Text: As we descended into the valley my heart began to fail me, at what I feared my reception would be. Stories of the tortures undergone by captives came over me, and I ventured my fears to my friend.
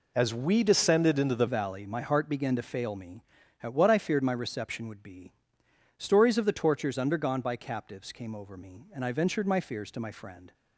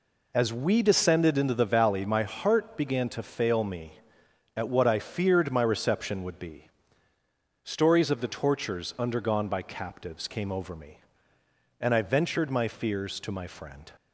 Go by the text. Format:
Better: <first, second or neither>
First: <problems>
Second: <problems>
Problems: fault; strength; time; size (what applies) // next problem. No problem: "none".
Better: second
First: changes voice at "valley"; from 1.4 s on; 9.1 s long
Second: none